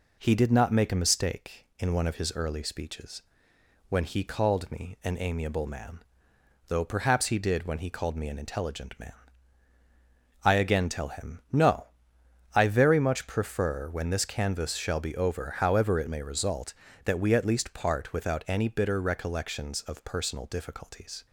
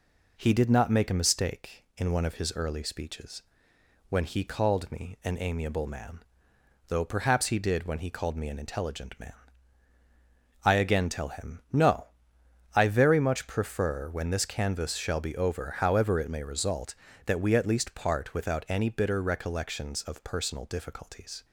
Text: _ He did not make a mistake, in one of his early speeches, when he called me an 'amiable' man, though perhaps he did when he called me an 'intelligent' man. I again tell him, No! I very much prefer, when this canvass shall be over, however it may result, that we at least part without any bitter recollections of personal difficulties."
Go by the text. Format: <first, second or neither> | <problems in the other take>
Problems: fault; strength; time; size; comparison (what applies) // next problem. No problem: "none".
neither | none